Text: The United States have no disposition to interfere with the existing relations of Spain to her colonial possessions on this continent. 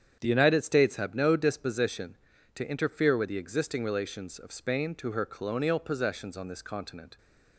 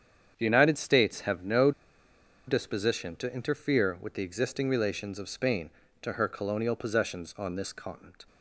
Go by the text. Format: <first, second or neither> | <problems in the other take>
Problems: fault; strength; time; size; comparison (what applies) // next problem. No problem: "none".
first | starts louder than the rest; strong; until 1.3 s; 8 dB; strong in the first // pauses between "no" and "disposition"; noticeable; at 1.7 s; 0.76 s long